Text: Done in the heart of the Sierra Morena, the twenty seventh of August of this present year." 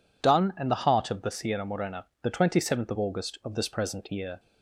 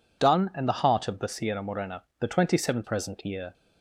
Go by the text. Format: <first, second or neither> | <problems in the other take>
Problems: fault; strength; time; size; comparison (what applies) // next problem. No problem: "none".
first | skips "of August of this"; at 2.8 s